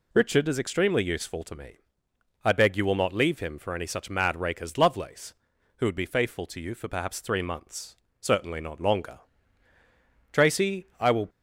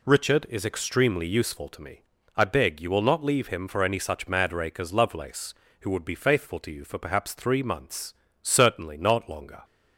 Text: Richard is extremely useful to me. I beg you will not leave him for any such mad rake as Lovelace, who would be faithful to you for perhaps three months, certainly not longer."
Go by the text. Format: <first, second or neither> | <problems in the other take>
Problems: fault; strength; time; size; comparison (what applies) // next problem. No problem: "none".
second | goes on to say "Tracy I will"; noticeable; from 10.3 s on; 0.96 s long